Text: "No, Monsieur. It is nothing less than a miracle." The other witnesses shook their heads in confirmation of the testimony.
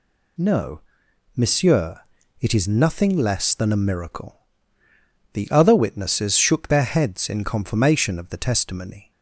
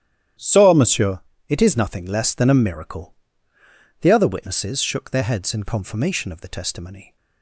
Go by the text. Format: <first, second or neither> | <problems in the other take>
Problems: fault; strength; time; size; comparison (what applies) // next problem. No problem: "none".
first | starts louder than the rest; strong; until 1.6 s; 11 dB // says "So" for "No"; at 0.3 s